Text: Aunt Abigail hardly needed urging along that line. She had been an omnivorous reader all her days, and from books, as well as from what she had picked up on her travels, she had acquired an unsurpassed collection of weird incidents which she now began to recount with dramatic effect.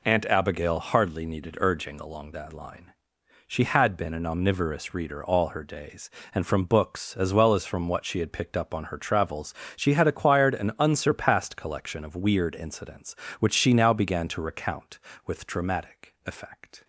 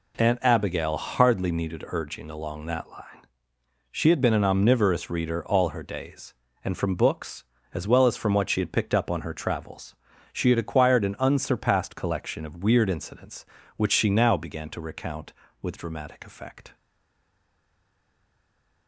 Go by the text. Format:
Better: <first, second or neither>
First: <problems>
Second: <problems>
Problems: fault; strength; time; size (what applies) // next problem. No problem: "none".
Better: first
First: none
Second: stays silent after the last word; from 16.7 s on; 2.1 s long